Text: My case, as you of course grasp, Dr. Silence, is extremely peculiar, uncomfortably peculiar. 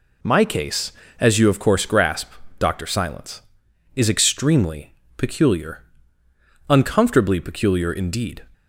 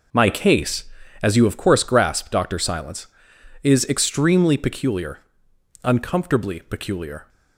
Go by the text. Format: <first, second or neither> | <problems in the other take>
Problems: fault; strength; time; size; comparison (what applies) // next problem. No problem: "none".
second | pauses between "extremely" and "peculiar"; slight; at 4.9 s; 0.16 s long // goes on to say "Indeed"; from 7.9 s on; 0.52 s long